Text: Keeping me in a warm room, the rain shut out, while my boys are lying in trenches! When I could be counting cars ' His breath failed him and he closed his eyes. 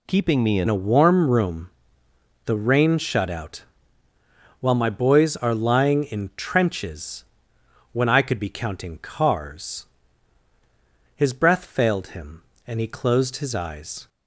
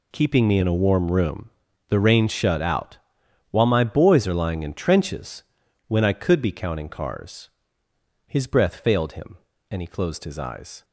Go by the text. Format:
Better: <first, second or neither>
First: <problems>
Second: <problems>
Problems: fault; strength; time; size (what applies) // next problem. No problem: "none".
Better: second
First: changes voice at "a"; from 0.6 s on; 13.4 s long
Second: none